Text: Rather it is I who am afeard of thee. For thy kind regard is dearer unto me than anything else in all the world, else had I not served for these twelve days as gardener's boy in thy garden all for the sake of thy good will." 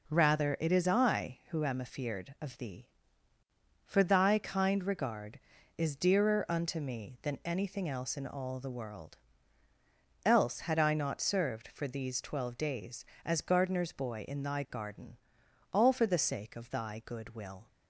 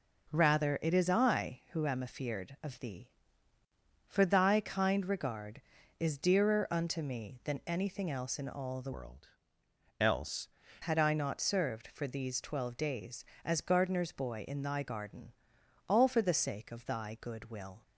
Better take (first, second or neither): first